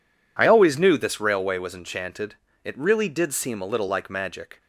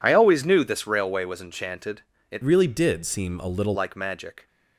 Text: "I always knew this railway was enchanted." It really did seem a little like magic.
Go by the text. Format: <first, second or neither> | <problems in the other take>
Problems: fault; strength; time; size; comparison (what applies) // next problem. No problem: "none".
first | changes voice from "really" to "little"; from 2.4 to 3.7 s; 1.3 s long